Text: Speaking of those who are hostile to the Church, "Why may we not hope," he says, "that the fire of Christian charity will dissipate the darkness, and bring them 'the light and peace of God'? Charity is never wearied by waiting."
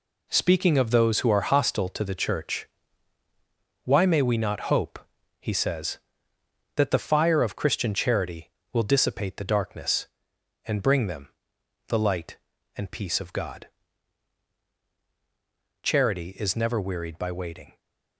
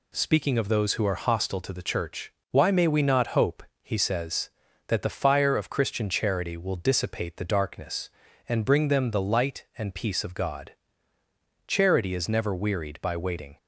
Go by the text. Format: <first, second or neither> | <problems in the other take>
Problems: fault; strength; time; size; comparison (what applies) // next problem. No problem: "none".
second | gets quieter; strong; throughout; 8.5 dB // pauses between "them" and "the"; noticeable; at 11.2 s; 0.56 s long